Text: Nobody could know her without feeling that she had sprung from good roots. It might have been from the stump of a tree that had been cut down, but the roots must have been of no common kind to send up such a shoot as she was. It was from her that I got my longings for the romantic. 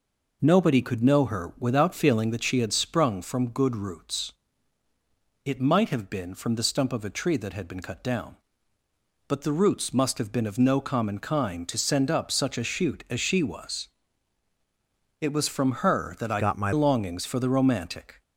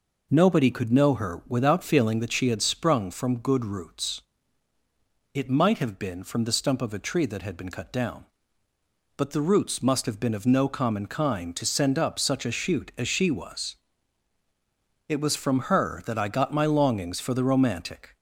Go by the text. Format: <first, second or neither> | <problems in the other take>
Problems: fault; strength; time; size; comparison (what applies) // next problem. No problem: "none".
second | changes voice from "got" to "my"; from 16.3 to 16.7 s; 0.4 s long